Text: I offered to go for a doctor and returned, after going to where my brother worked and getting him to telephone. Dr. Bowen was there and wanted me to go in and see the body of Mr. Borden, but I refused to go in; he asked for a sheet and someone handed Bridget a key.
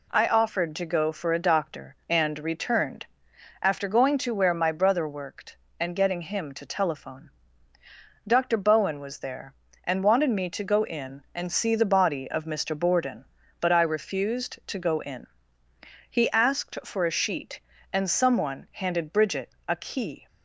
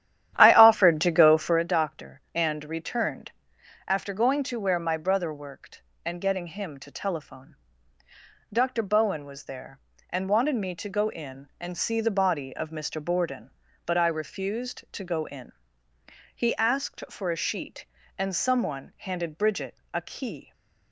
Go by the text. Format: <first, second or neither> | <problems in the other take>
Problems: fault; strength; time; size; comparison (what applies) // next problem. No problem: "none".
first | starts louder than the rest; strong; until 1.6 s; 11.5 dB // pauses between "Bridget" and "a"; slight; at 19.7 s; 0.16 s long; slight in the first